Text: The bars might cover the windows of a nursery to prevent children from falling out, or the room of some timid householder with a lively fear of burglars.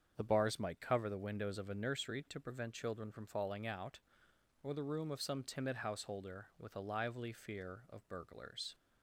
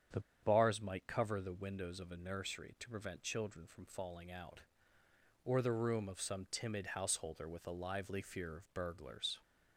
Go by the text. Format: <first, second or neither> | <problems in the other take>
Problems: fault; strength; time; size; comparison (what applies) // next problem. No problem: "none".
first | starts louder than the rest; strong; until 1.3 s; 8.5 dB; strong in the first // pauses between "The" and "bars"; slight; at 0.1 s; 0.22 s long